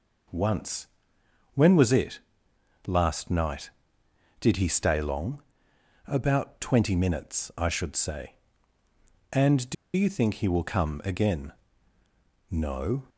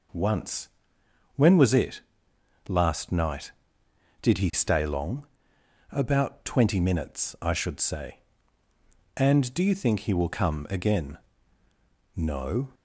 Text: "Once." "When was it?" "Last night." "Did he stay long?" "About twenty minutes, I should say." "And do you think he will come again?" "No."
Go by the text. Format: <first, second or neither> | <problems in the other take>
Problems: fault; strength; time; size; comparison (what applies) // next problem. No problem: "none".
second | pauses between "do" and "you"; slight; at 9.7 s; 0.21 s long